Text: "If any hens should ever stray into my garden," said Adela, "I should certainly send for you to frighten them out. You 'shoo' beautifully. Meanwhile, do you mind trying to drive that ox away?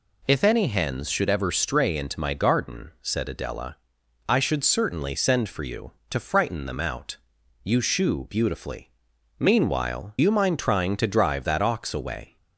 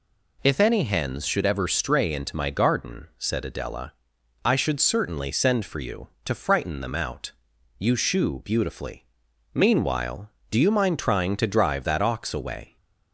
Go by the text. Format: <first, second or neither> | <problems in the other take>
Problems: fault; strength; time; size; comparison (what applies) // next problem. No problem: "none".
second | skips "do"; at 10.1 s